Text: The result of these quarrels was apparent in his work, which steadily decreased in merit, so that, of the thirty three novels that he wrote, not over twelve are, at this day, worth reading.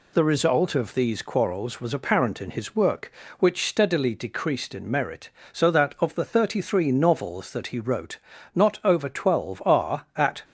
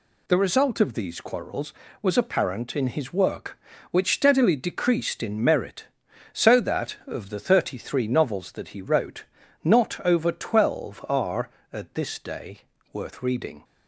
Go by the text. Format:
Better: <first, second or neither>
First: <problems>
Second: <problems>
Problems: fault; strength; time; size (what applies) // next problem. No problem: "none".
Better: second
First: stops before "this day worth reading"; at 10.4 s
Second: none